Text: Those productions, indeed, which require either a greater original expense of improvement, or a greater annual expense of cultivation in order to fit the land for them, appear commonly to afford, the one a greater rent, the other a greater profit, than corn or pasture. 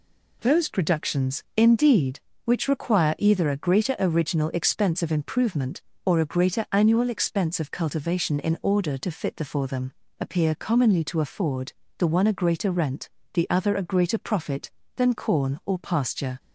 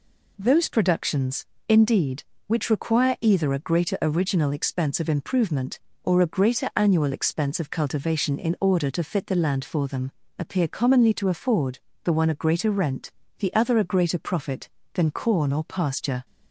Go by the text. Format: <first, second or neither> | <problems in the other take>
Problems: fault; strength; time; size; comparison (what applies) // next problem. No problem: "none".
second | skips "land"; at 9.4 s